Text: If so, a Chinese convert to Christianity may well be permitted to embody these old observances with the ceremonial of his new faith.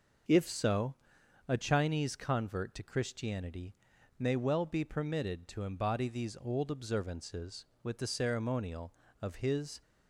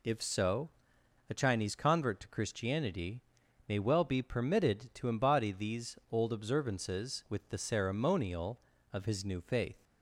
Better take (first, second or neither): second